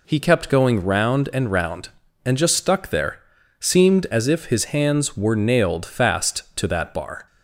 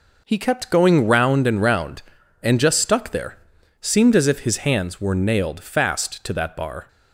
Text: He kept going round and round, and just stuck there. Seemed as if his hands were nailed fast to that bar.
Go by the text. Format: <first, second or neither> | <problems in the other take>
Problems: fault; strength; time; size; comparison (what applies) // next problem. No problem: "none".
first | gets quieter; strong; throughout; 8 dB